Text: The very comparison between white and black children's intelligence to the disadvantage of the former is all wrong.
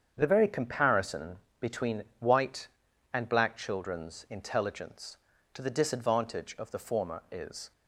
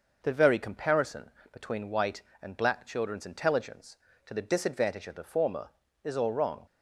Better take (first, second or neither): second